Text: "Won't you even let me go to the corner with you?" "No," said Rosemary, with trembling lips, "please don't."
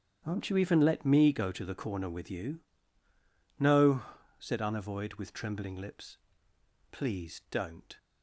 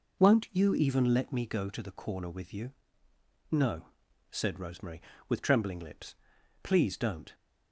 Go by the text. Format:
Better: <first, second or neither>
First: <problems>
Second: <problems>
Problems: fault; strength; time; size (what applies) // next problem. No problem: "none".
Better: second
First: starts louder than the rest; strong; until 1.2 s; 8.5 dB // says "Unavoid" for "Rosemary"; at 4.6 s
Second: none